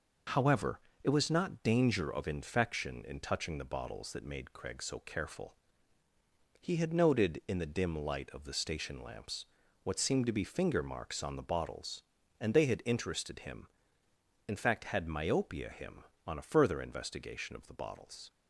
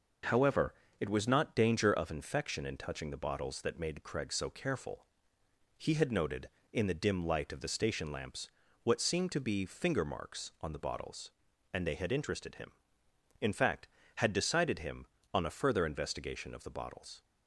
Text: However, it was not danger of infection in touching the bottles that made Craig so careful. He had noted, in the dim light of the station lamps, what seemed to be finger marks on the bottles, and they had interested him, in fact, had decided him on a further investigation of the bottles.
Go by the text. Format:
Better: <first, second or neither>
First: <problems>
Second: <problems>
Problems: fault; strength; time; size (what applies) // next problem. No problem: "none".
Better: second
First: says "myopia" for "decided"; at 15.0 s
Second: none